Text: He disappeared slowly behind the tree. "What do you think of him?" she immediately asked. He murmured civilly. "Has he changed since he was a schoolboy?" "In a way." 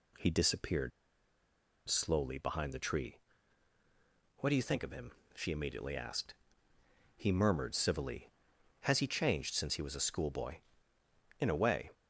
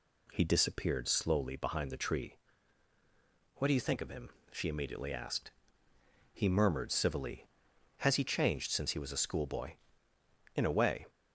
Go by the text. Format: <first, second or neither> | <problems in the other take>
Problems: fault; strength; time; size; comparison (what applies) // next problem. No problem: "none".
second | pauses between "disappeared" and "slowly"; at 0.9 s; 0.98 s long